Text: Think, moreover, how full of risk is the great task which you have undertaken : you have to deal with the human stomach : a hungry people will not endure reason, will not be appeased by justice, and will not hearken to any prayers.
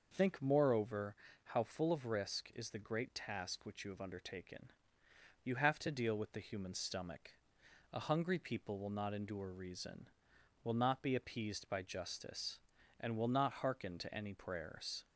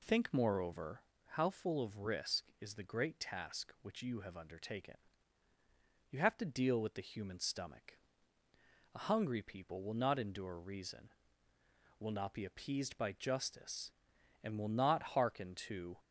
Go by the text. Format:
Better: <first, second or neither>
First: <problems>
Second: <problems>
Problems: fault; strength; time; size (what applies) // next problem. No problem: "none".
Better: first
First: none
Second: stops before "any prayers"; at 15.9 s